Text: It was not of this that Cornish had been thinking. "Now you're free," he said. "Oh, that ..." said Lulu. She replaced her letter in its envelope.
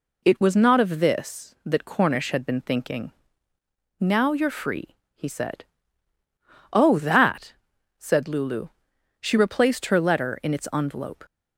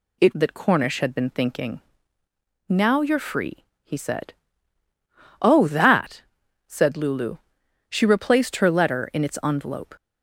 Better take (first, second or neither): first